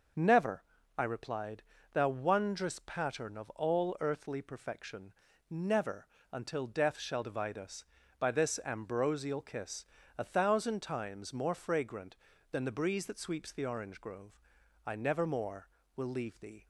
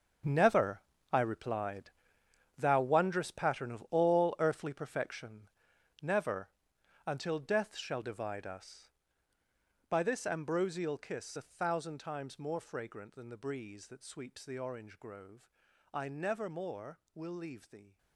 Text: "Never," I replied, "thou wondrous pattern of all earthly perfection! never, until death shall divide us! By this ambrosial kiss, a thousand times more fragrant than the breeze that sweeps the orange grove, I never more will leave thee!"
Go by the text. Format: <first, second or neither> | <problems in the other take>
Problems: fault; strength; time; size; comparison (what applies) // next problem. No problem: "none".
first | gets quieter; strong; throughout; 14 dB